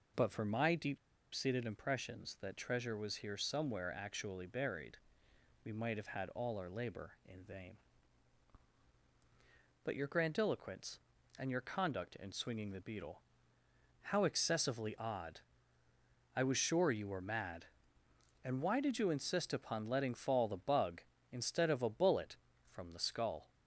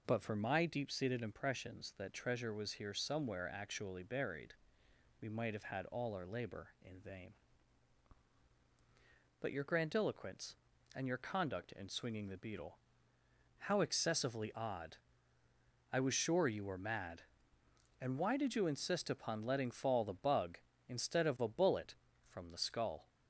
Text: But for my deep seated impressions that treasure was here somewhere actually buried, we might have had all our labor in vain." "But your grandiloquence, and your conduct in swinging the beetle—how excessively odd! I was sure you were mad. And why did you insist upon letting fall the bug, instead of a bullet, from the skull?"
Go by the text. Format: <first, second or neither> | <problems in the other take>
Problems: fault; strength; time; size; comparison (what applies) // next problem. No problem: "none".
second | pauses between "deep" and "seated"; at 0.9 s; 0.37 s long